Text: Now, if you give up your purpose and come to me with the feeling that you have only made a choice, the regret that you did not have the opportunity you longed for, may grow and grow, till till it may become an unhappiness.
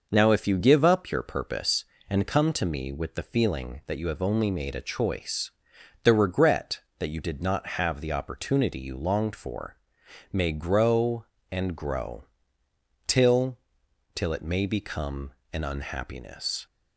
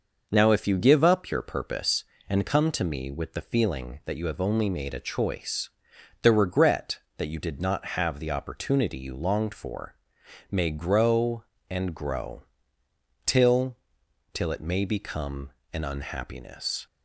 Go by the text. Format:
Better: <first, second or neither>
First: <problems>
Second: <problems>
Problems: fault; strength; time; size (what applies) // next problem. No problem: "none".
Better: neither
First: pauses between "till" and "till"; noticeable; at 13.5 s; 0.58 s long // pauses between "become" and "an"; slight; at 15.3 s; 0.22 s long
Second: pauses between "till" and "till"; noticeable; at 13.7 s; 0.58 s long // pauses between "become" and "an"; slight; at 15.4 s; 0.24 s long